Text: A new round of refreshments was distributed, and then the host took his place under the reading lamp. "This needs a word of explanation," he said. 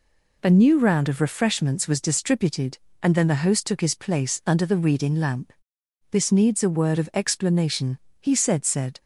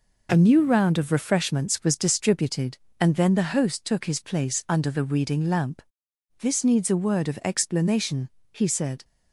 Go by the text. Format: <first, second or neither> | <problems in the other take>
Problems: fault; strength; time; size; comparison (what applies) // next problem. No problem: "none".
second | says "said" twice; at 8.6 s